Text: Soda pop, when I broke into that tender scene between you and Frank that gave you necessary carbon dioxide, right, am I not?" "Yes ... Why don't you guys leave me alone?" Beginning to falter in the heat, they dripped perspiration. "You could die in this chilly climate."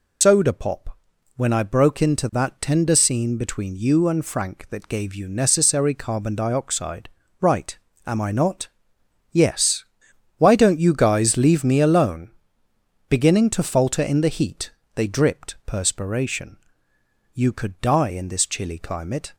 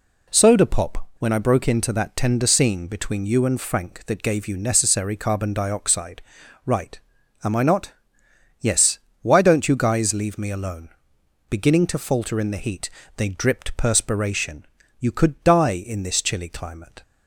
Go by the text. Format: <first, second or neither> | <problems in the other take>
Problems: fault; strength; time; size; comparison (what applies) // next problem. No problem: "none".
second | loses the start of "Soda"; at 0.2 s; 95 ms